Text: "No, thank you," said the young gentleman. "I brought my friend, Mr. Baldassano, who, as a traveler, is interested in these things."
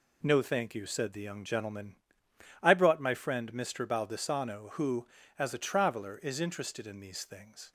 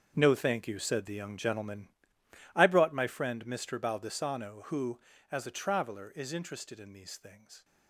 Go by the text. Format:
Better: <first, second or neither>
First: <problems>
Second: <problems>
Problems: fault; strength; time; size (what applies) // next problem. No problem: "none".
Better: first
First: none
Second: gets quieter; strong; throughout; 14 dB